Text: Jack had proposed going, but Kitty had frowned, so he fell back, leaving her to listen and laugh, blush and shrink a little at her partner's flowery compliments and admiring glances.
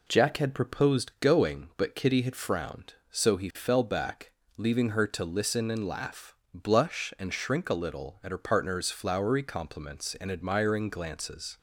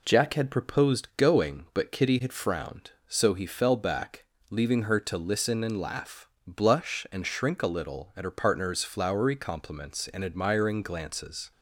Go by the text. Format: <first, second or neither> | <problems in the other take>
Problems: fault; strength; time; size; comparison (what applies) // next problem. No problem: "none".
neither | none